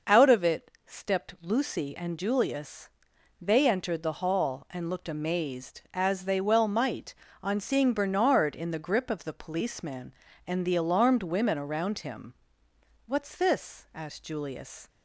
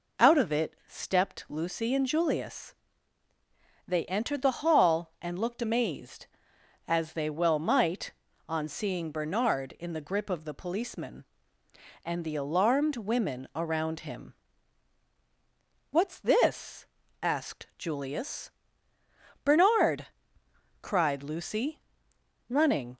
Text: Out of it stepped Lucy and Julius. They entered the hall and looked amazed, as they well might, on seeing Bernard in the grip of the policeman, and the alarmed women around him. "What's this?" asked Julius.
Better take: first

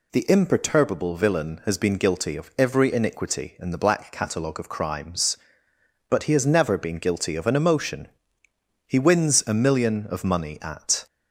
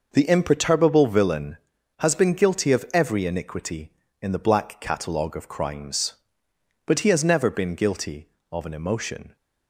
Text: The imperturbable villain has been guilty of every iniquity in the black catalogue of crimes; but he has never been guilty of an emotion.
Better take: second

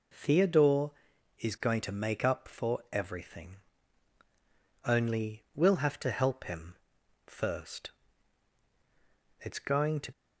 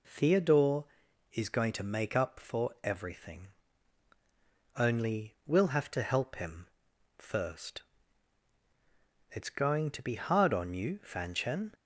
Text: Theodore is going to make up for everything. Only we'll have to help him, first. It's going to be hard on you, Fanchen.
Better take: second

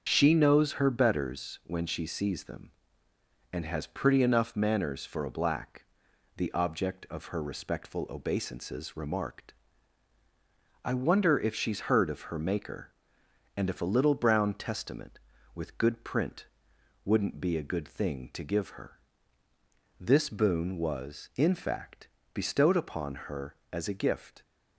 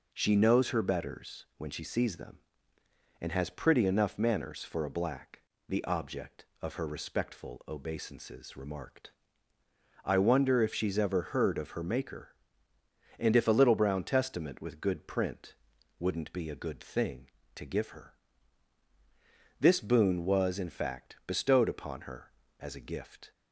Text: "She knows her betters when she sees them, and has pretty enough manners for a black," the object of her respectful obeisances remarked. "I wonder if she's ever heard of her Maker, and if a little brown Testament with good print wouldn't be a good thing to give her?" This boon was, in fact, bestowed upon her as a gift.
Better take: second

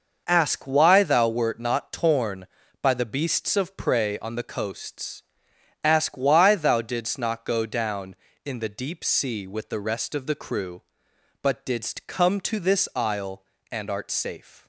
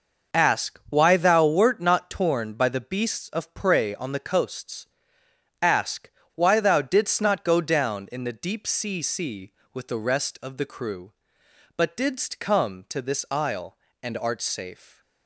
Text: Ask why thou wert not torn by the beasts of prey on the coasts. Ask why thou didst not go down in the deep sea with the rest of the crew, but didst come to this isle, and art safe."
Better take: first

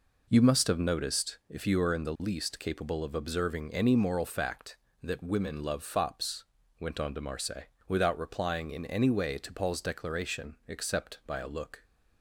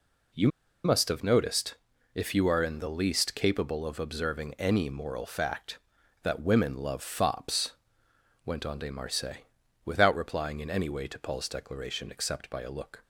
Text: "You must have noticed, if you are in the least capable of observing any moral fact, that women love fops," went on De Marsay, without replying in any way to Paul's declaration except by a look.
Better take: first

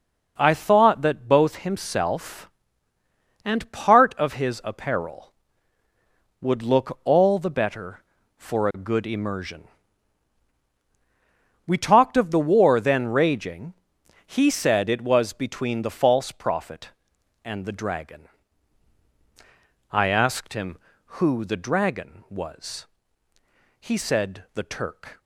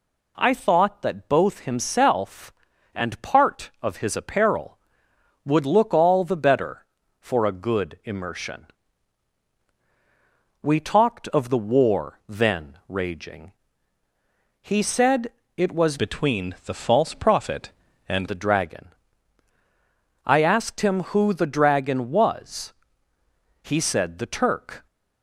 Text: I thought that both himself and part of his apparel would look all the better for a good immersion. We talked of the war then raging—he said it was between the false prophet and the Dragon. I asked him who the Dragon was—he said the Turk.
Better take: first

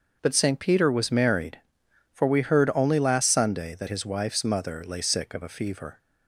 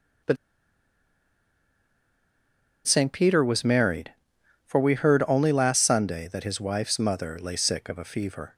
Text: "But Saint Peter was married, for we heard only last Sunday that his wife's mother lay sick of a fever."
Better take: first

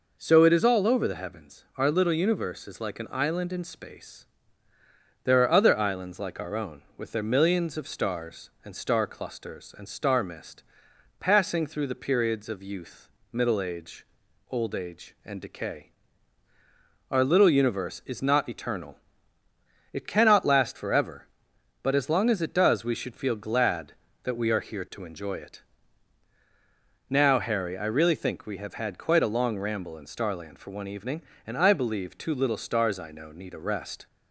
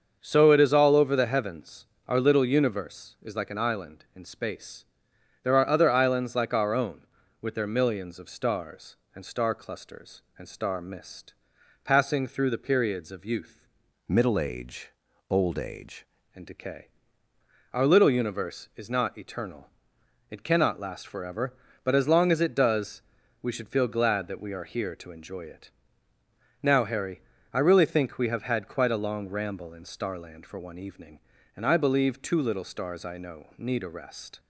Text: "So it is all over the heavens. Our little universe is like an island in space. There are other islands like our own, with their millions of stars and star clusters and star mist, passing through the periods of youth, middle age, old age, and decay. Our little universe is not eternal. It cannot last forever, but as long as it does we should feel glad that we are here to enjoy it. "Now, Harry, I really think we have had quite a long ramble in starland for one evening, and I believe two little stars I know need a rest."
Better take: first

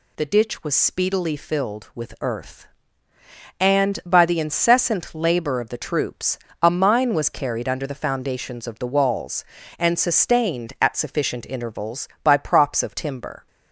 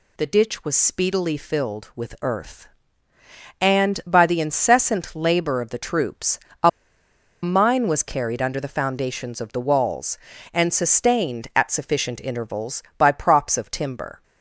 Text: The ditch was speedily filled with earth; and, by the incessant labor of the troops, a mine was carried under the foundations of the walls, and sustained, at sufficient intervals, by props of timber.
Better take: first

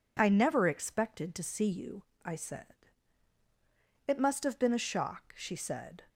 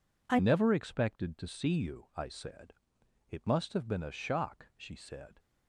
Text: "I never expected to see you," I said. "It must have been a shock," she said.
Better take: first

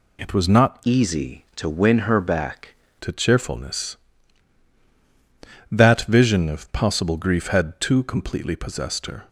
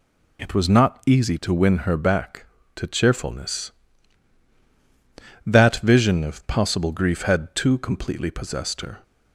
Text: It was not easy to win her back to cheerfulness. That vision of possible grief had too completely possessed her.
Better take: second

